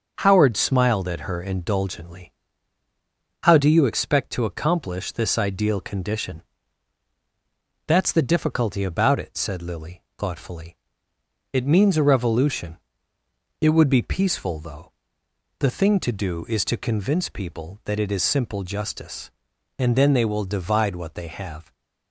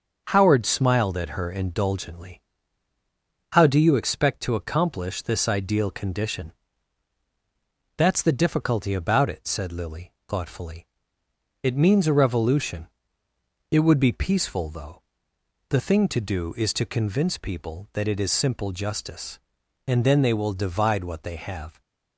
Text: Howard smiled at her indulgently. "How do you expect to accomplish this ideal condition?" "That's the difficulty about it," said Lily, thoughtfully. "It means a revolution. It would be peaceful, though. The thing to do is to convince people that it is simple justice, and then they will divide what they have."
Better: neither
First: starts louder than the rest; until 1.2 s; 6.5 dB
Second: starts louder than the rest; until 1.2 s; 6.5 dB

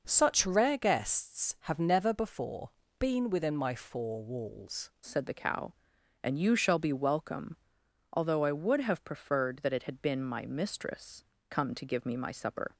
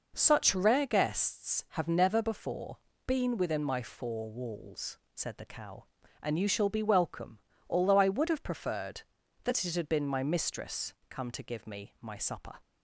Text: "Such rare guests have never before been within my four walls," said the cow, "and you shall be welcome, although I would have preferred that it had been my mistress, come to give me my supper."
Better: second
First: pauses between "before" and "been"; slight; at 2.6 s; 0.30 s long // changes voice at "said"; from 5.0 s on; 7.7 s long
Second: pauses between "before" and "been"; slight; at 2.7 s; 0.30 s long

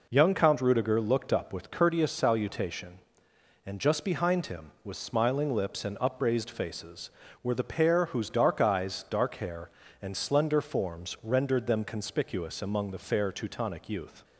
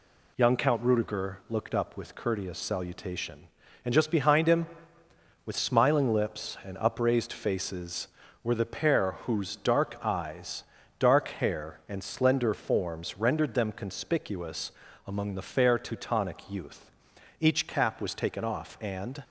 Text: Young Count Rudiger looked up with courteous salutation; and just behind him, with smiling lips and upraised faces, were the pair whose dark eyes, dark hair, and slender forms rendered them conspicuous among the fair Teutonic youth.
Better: first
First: none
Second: pauses between "conspicuous" and "among"; slight; at 14.7 s; 0.34 s long // goes on to say "Each cap was taken off and"; strong; from 17.3 s on; 1.8 s long

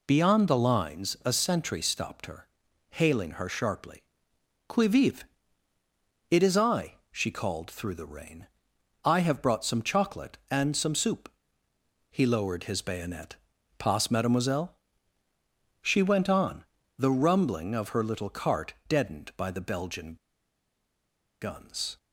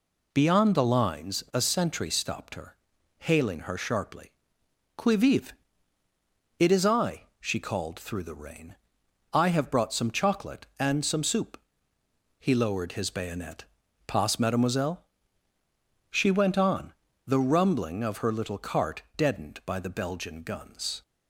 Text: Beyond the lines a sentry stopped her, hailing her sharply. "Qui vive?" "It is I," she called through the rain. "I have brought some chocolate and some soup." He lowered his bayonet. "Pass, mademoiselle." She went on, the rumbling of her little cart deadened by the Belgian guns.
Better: second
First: pauses between "cart" and "deadened"; slight; at 18.7 s; 0.16 s long // pauses between "Belgian" and "guns"; strong; at 20.1 s; 1.2 s long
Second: pauses between "cart" and "deadened"; slight; at 19.0 s; 0.16 s long

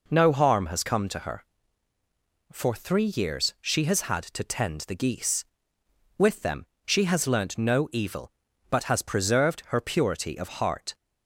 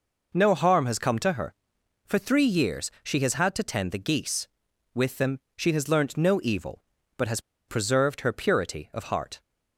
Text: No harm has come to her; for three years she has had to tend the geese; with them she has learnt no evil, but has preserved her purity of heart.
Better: first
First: pauses between "them" and "she"; slight; at 6.6 s; 0.18 s long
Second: pauses between "them" and "she"; slight; at 5.3 s; 0.18 s long // pauses between "has" and "preserved"; slight; at 7.4 s; 0.28 s long

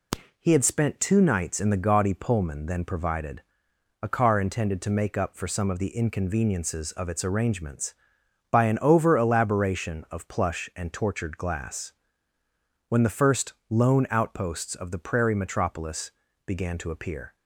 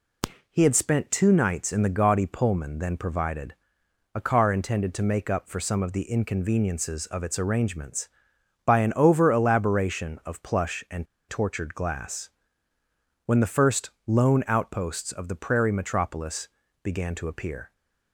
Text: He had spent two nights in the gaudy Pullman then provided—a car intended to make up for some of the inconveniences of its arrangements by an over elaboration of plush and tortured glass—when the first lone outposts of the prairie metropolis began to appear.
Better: first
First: pauses between "first" and "lone"; slight; at 13.5 s; 0.16 s long // pauses between "metropolis" and "began"; slight; at 16.1 s; 0.34 s long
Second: pauses between "and" and "tortured"; slight; at 11.0 s; 0.23 s long // pauses between "first" and "lone"; slight; at 13.8 s; 0.16 s long // pauses between "metropolis" and "began"; slight; at 16.4 s; 0.34 s long

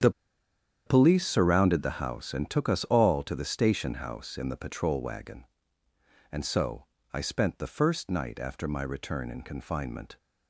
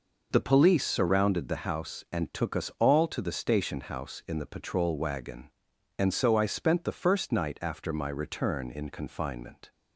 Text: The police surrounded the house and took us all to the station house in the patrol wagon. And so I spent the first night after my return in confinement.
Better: second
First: starts louder than the rest; strong; until 1.7 s; 8.5 dB // pauses between "The" and "police"; noticeable; at 0.1 s; 0.75 s long // pauses between "so" and "I"; slight; at 6.8 s; 0.30 s long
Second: none

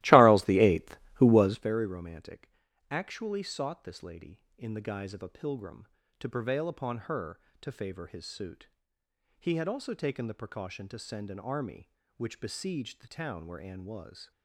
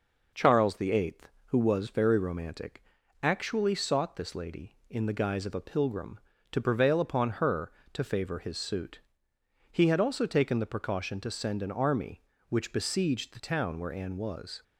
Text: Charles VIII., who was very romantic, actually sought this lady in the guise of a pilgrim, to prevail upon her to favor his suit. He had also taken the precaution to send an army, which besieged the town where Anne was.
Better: second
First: starts louder than the rest; strong; until 1.8 s; 17 dB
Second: none

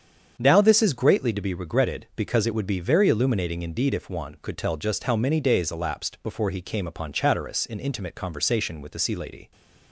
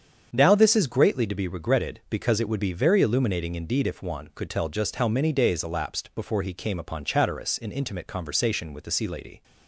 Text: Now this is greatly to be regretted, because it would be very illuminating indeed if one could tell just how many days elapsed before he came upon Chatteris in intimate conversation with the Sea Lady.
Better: neither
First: starts louder than the rest; strong; until 1.4 s; 7.5 dB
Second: starts louder than the rest; strong; until 1.3 s; 7.5 dB

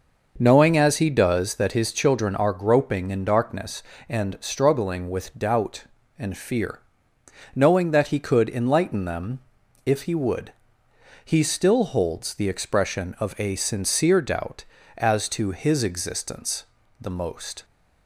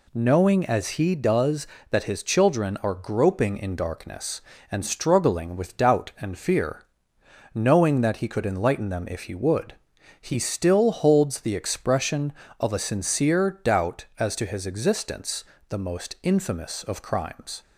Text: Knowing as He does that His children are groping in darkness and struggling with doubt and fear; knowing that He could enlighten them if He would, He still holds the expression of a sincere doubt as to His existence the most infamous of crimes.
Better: second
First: starts louder than the rest; noticeable; until 1.3 s; 6 dB // pauses between "them" and "if"; noticeable; at 9.3 s; 0.48 s long // pauses between "existence" and "the"; slight; at 16.6 s; 0.36 s long // stops before "infamous of crimes"; at 17.6 s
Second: pauses between "existence" and "the"; slight; at 15.4 s; 0.24 s long

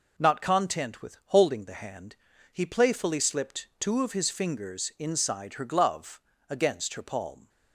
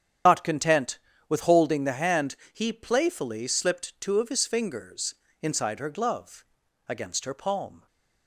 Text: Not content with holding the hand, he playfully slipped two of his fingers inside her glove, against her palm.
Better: first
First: none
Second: loses the start of "Not"; at 0.2 s; 65 ms // starts louder than the rest; strong; until 1.5 s; 9 dB // pauses between "fingers" and "inside"; slight; at 5.1 s; 0.28 s long

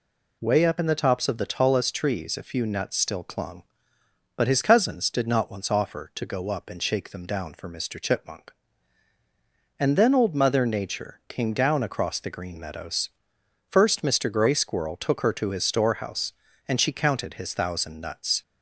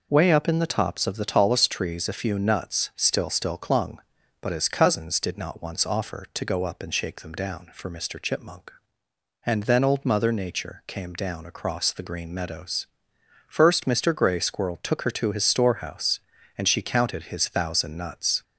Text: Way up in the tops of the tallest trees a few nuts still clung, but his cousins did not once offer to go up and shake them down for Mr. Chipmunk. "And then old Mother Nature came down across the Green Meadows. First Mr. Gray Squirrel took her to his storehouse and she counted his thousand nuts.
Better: first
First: none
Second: says "still" twice; at 3.2 s

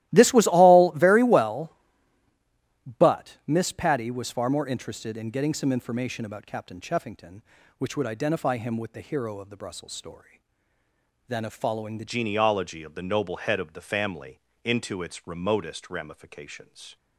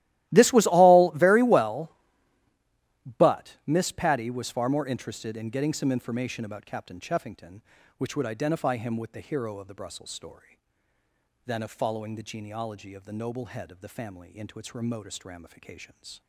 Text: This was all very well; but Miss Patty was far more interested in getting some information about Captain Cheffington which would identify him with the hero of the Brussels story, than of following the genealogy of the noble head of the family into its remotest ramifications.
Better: second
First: starts louder than the rest; strong; until 1.1 s; 16 dB // changes voice at "genealogy"; from 12.0 s on; 4.9 s long // pauses between "family" and "into"; slight; at 14.3 s; 0.24 s long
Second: starts louder than the rest; strong; until 1.3 s; 15.5 dB

